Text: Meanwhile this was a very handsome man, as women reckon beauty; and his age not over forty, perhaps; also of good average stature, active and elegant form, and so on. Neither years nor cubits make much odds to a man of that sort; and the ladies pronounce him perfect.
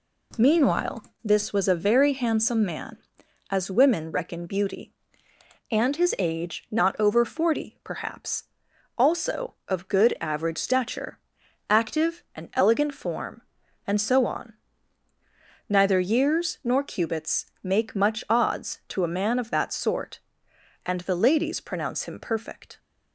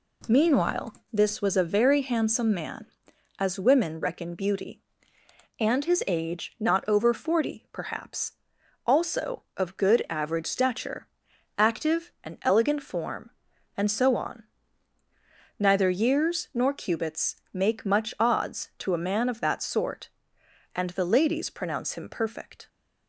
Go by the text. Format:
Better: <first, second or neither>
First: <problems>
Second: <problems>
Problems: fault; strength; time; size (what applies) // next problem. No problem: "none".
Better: neither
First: pauses between "Meanwhile" and "this"; slight; at 1.0 s; 0.20 s long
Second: pauses between "Meanwhile" and "this"; slight; at 0.9 s; 0.18 s long